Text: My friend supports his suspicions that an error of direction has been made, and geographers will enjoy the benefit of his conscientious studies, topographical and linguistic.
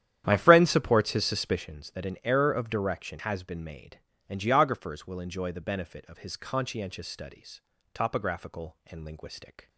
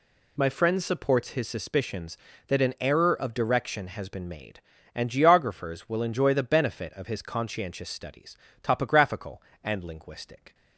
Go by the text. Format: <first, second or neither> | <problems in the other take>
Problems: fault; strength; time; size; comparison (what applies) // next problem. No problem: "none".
second | starts louder than the rest; strong; until 1.7 s; 10.5 dB